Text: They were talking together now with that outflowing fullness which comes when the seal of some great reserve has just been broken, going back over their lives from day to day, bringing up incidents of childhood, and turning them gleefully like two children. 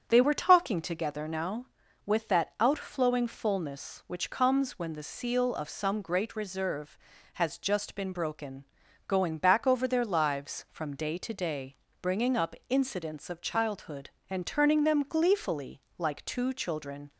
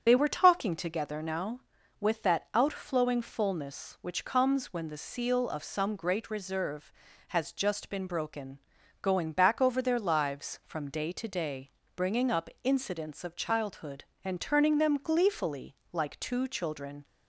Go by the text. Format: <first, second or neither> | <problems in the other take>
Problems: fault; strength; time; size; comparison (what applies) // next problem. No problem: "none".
first | loses the start of "They"; at 0.0 s; 30 ms // starts louder than the rest; strong; until 1.0 s; 8 dB; strong in the first // pauses between "gleefully" and "like"; slight; at 15.7 s; 0.16 s long; slight in the first